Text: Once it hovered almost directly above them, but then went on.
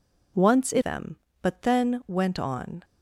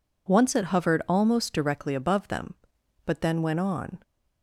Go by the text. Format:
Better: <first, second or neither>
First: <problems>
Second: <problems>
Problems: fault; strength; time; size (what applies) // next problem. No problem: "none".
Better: second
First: skips "hovered almost directly above"; at 0.8 s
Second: none